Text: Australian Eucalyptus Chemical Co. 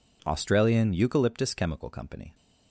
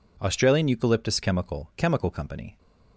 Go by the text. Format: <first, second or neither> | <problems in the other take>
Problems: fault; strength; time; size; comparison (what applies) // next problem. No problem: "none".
first | says "Chemical" twice; at 1.7 s